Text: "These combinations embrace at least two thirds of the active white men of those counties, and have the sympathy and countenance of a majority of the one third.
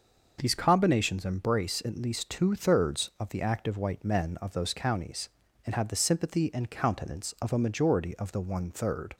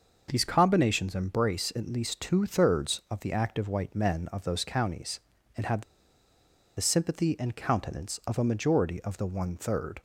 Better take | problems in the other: first | starts louder than the rest; noticeable; until 1.3 s; 6 dB; noticeable in the first // pauses between "have" and "the"; noticeable; at 5.8 s; 0.95 s long

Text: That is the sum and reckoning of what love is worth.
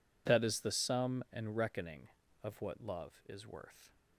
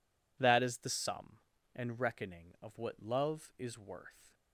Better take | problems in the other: neither | none

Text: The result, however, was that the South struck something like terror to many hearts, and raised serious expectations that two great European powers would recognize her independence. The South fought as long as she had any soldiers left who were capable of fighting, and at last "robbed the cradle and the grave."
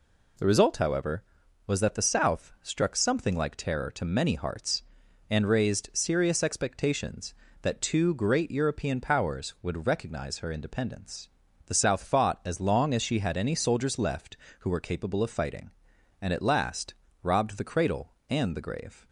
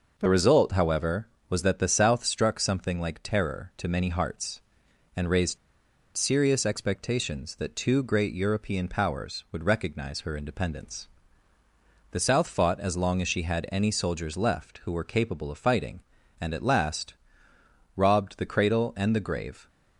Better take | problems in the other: first | pauses between "raised" and "serious"; noticeable; at 5.5 s; 0.59 s long // pauses between "last" and "robbed"; noticeable; at 17.1 s; 0.82 s long; slight in the first

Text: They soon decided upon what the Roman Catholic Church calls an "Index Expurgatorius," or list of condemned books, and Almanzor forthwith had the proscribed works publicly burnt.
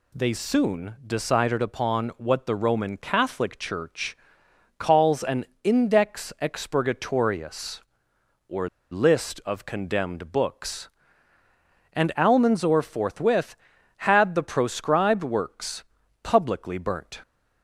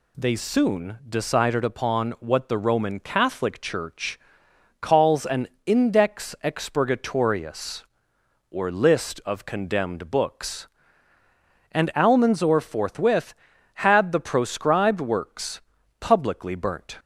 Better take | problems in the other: second | pauses between "Church" and "calls"; noticeable; at 4.1 s; 0.62 s long; noticeable in the second // pauses between "an" and "Index"; slight; at 5.4 s; 0.18 s long; slight in the second // pauses between "or" and "list"; slight; at 8.6 s; 0.23 s long // pauses between "works" and "publicly"; at 15.8 s; 0.38 s long; also in the second

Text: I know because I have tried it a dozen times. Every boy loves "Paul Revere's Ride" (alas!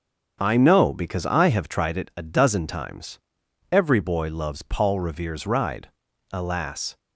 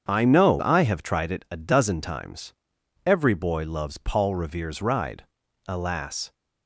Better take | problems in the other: first | starts louder than the rest; strong; until 1.0 s; 7.5 dB; strong in the first // skips "because"; at 0.6 s

